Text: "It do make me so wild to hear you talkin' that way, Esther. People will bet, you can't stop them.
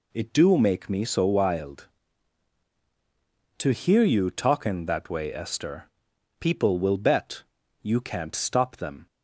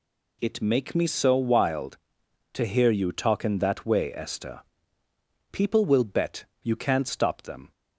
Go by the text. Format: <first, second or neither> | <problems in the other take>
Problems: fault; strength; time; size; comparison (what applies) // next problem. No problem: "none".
first | skips "do"; at 0.6 s